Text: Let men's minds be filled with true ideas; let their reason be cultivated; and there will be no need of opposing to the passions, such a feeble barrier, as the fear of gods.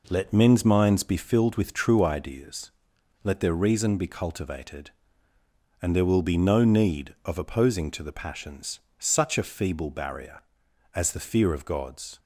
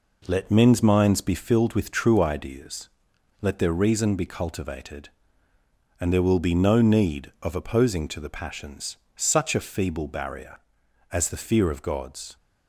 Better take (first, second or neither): neither